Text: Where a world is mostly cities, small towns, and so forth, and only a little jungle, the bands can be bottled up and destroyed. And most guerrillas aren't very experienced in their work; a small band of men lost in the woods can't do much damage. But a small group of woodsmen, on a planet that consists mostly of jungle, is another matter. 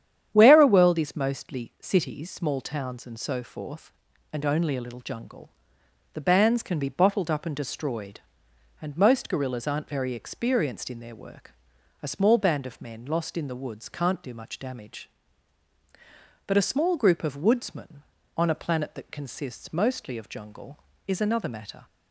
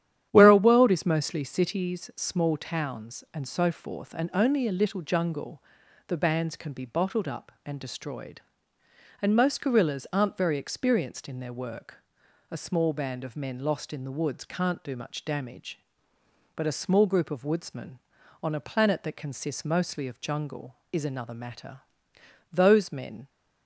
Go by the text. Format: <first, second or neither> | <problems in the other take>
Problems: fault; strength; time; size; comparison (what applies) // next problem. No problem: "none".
first | starts louder than the rest; strong; until 1.3 s; 10.5 dB; strong in the first // goes on to say "Those men"; noticeable; from 22.5 s on; 0.76 s long